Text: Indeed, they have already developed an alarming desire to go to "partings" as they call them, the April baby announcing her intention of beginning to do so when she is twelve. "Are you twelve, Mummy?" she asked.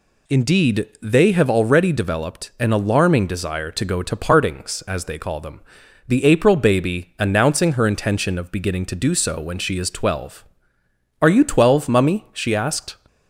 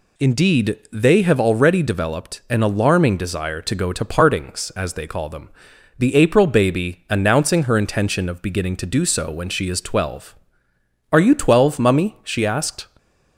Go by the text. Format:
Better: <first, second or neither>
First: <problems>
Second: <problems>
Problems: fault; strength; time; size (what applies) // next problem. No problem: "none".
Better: neither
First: none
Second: none